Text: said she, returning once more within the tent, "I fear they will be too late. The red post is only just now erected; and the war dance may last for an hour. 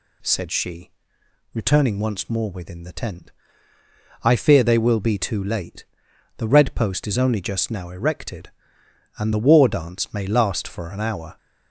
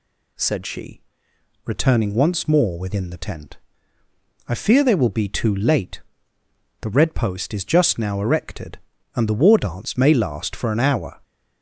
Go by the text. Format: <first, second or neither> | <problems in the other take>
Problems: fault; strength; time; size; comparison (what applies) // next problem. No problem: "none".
first | skips "only"; at 7.6 s